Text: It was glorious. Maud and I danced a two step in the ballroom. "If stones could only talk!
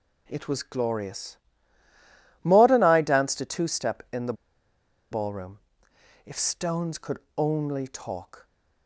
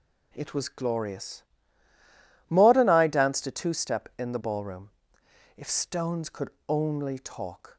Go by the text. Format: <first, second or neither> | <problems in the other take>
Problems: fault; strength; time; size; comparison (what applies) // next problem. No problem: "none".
second | pauses between "the" and "ballroom"; noticeable; at 4.3 s; 0.77 s long // pauses between "could" and "only"; slight; at 7.1 s; 0.18 s long; slight in the second